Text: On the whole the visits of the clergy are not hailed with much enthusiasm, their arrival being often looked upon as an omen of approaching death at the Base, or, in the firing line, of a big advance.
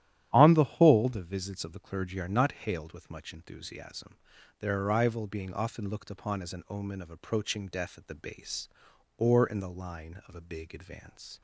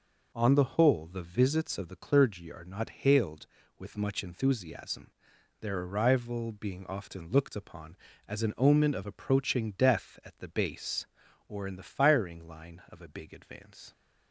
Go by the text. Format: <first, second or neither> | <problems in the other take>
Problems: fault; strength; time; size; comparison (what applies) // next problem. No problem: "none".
second | starts louder than the rest; strong; until 1.3 s; 12 dB // skips "firing"; at 9.6 s